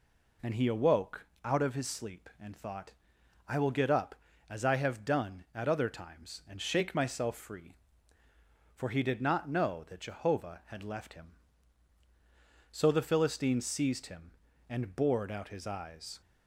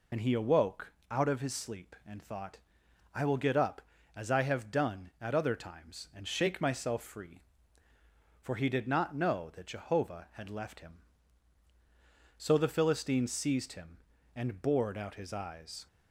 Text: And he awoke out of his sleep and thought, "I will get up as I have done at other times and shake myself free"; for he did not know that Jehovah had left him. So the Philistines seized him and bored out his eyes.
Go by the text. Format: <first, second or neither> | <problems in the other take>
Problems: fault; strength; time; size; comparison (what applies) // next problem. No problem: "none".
first | loses the start of "And"; at 0.1 s; 45 ms // pauses between "awoke" and "out"; slight; at 0.9 s; 0.18 s long; slight in the first